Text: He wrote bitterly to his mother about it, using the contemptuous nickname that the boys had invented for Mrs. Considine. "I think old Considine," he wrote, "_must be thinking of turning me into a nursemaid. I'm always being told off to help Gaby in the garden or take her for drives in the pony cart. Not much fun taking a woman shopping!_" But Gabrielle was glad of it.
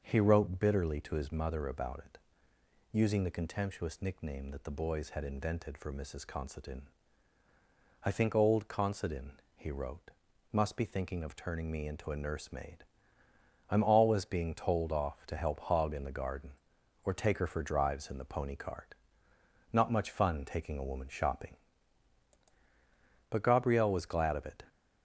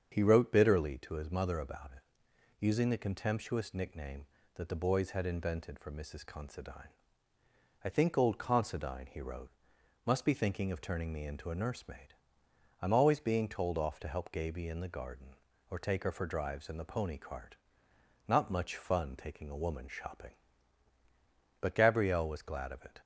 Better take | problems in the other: second | starts louder than the rest; until 1.0 s; 6.5 dB; strong in the second // says "Hog" for "Gaby"; at 15.6 s

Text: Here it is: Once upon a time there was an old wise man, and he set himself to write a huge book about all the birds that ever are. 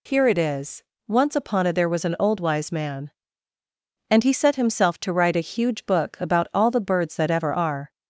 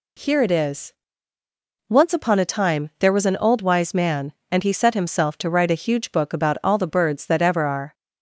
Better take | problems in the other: second | skips "time"; at 1.7 s

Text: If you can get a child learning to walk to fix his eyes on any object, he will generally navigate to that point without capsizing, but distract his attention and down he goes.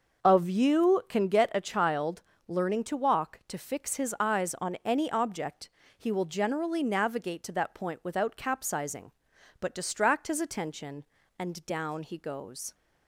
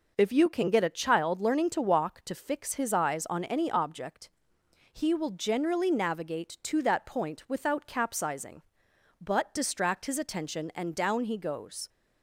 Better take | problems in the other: second | starts louder than the rest; noticeable; until 1.3 s; 6 dB // says "Of" for "If"; at 0.2 s // pauses between "child" and "learning"; slight; at 2.2 s; 0.26 s long

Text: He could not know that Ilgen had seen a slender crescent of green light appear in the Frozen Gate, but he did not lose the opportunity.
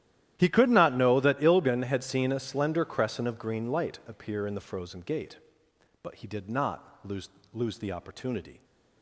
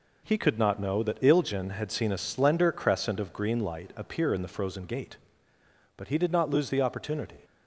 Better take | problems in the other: second | starts louder than the rest; strong; until 1.3 s; 12.5 dB // says "lose" twice; at 7.5 s

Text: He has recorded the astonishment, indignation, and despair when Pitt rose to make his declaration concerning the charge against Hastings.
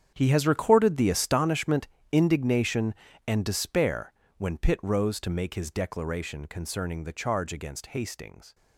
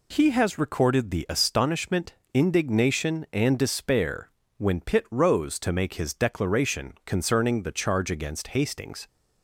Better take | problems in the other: second | gets quieter; strong; throughout; 15.5 dB // pauses between "despair" and "when"; slight; at 4.1 s; 0.24 s long; slight in the second

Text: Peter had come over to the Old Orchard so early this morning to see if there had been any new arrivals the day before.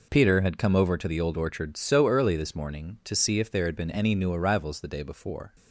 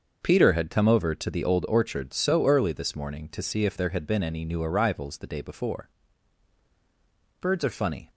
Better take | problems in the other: first | starts louder than the rest; until 1.2 s; 6.5 dB // goes on to say "Birds are funny"; noticeable; from 7.3 s on; 0.70 s long

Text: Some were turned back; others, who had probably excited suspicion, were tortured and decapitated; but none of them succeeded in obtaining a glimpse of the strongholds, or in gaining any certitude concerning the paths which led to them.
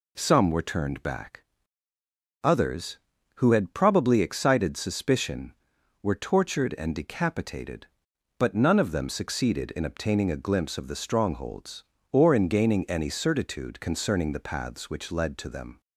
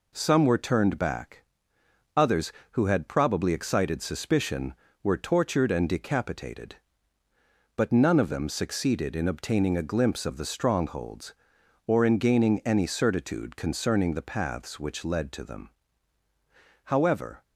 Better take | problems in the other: first | goes on to say "However"; from 16.8 s on; 0.58 s long

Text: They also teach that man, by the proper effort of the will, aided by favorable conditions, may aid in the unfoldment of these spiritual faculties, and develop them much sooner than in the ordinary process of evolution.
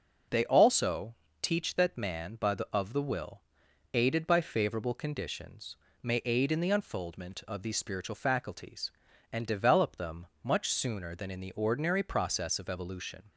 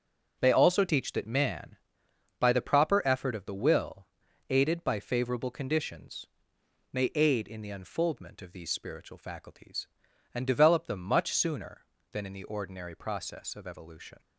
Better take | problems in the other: second | pauses between "also" and "teach"; slight; at 1.1 s; 0.26 s long // skips "proper effort"; at 2.6 s // pauses between "them" and "much"; slight; at 10.2 s; 0.18 s long

